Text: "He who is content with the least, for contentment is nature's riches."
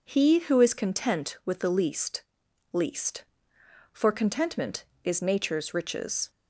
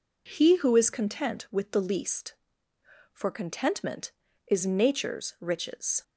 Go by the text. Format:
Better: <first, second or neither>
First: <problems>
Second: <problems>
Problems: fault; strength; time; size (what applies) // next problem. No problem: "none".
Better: second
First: says "least" twice; at 2.7 s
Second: none